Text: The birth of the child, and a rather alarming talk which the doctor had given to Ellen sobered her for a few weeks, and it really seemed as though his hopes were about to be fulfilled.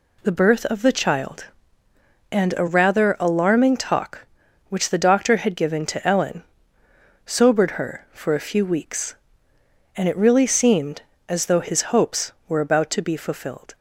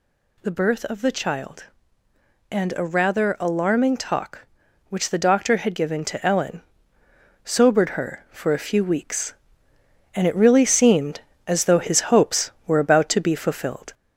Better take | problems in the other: first | gets louder; slight; throughout; 2 dB // pauses between "Ellen" and "sobered"; noticeable; at 6.6 s; 0.82 s long; noticeable in the first

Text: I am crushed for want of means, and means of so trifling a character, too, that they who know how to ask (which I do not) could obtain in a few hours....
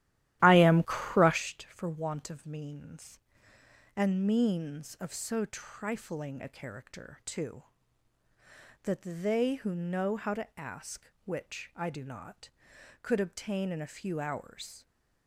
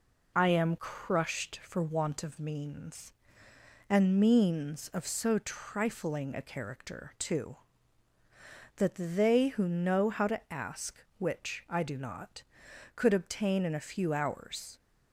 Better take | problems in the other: second | starts louder than the rest; strong; until 1.4 s; 13.5 dB

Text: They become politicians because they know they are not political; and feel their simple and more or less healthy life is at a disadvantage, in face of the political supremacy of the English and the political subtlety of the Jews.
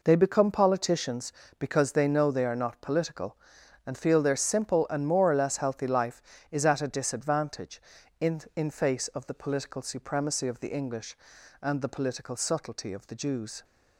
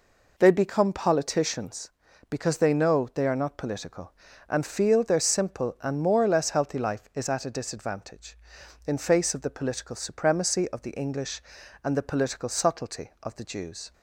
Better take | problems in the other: second | says "in" twice; at 8.5 s

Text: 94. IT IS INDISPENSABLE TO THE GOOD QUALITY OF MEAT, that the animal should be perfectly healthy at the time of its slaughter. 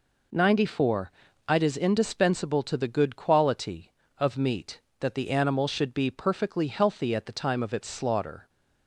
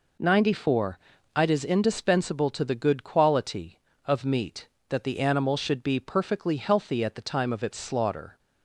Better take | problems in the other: neither | none

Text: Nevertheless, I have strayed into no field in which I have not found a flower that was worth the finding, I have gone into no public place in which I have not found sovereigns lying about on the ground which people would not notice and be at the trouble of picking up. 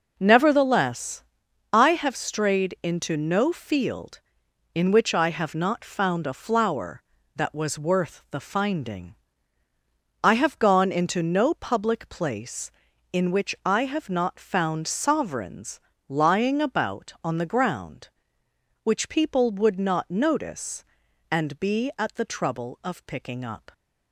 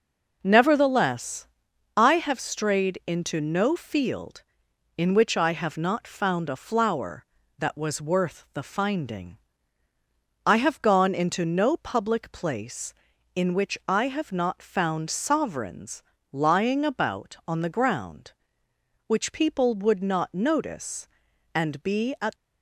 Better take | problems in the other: first | pauses between "sovereigns" and "lying"; slight; at 16.0 s; 0.30 s long; slight in the first // stops before "the trouble of picking up"; at 22.3 s

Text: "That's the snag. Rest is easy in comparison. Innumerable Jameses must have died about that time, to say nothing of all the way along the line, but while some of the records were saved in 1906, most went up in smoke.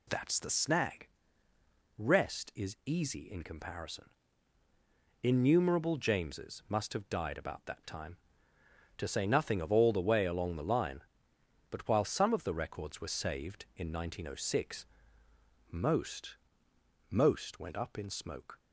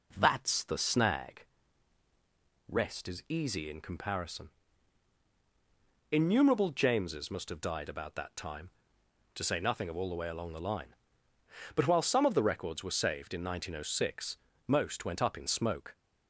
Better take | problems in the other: second | says "most" twice; at 17.1 s

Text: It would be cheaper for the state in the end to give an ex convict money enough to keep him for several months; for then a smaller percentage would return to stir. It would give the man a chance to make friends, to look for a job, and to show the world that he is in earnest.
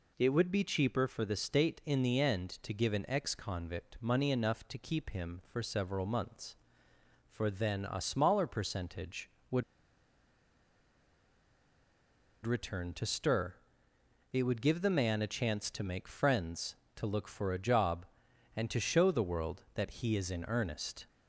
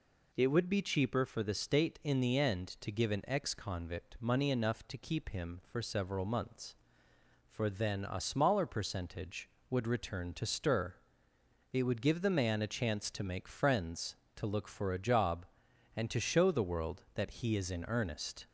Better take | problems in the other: second | pauses between "would" and "return"; strong; at 9.6 s; 2.8 s long

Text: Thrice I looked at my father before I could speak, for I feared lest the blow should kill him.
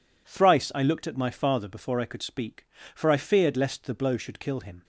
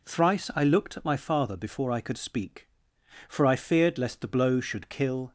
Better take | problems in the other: first | stops before "him"; at 5.2 s

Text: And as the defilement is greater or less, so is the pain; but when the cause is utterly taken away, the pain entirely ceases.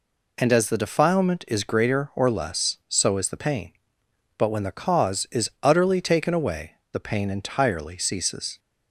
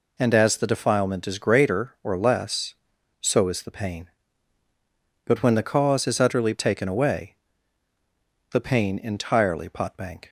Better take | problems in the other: first | says "potbank" for "ceases"; at 9.6 s

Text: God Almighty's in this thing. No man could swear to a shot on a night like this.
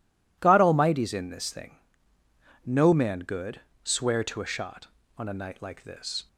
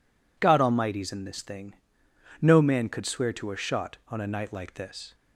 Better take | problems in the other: second | says "good" for "could"; at 3.1 s

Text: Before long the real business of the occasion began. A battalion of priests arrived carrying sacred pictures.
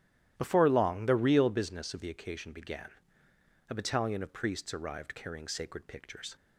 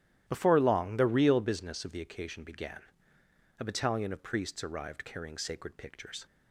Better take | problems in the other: neither | starts louder than the rest; strong; the same in both

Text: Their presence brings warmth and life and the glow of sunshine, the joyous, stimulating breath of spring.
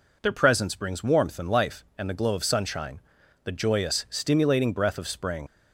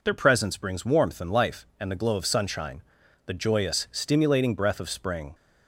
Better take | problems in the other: second | leaves "spring" unfinished; at 5.4 s; 60 ms

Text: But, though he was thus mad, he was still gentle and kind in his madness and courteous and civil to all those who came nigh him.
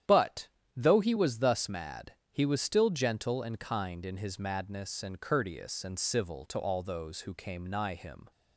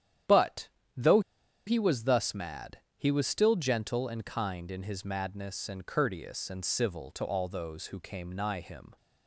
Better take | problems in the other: first | starts louder than the rest; strong; until 2.0 s; 10 dB; strong in the first // pauses between "though" and "he"; noticeable; at 1.1 s; 0.46 s long

